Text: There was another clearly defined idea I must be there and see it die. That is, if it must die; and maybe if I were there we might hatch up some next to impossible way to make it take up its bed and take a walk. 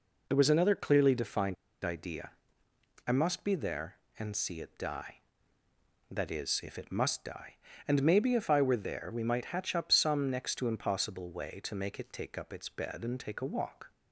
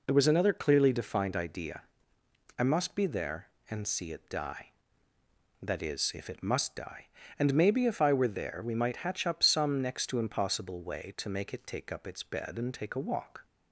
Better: second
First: pauses between "defined" and "idea"; slight; at 1.5 s; 0.29 s long // pauses between "idea" and "I"; noticeable; at 2.3 s; 0.76 s long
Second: pauses between "idea" and "I"; noticeable; at 1.8 s; 0.76 s long

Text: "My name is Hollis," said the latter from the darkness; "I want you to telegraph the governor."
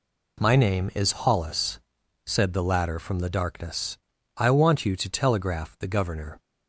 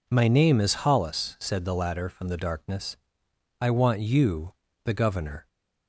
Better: first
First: none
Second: skips "to telegraph"; at 4.6 s

